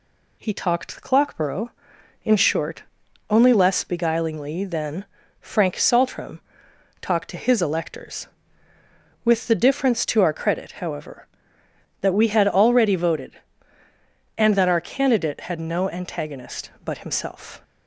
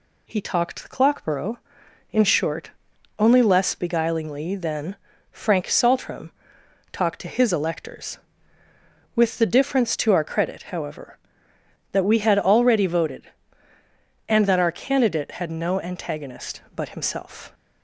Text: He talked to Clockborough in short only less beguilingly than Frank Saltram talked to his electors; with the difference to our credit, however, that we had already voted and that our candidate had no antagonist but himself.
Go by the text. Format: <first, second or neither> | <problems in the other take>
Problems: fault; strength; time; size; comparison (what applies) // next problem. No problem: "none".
neither | pauses between "short" and "only"; the same in both // pauses between "than" and "Frank"; slight; the same in both // pauses between "Saltram" and "talked"; noticeable; the same in both